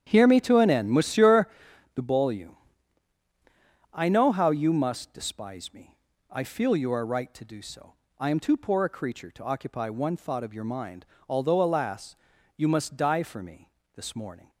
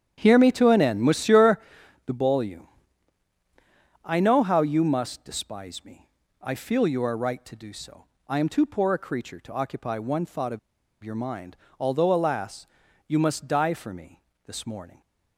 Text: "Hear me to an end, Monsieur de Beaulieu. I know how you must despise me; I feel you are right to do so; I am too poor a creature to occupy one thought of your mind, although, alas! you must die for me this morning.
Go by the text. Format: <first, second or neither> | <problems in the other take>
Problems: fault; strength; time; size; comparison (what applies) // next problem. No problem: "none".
first | starts louder than the rest; strong; until 1.1 s; 9.5 dB; strong in the first // pauses between "Monsieur" and "de"; noticeable; at 1.5 s; 0.46 s long; noticeable in the first // pauses between "of" and "your"; at 10.5 s; 0.43 s long // pauses between "me" and "this"; slight; at 14.2 s; 0.24 s long; slight in the first